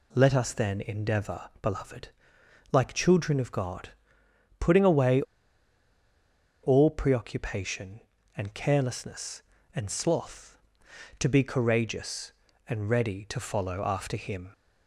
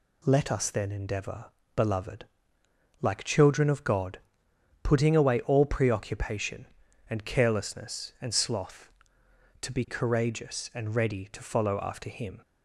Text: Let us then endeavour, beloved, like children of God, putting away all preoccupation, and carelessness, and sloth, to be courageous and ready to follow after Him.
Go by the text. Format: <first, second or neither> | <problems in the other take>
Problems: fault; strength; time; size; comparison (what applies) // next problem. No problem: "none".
second | pauses between "away" and "all"; strong; at 5.2 s; 1.4 s long